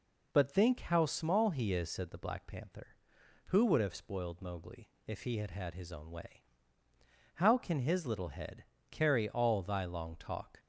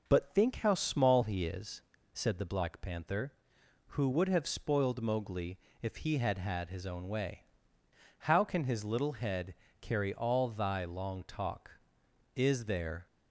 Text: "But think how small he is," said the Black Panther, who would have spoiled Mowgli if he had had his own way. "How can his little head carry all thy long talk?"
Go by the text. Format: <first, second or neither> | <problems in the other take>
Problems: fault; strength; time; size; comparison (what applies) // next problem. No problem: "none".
first | pauses between "Mowgli" and "if"; slight; at 5.5 s; 0.22 s long; slight in the first // pauses between "head" and "carry"; slight; at 9.5 s; 0.26 s long; slight in the first // goes on to say "Is there"; noticeable; from 12.3 s on; 0.72 s long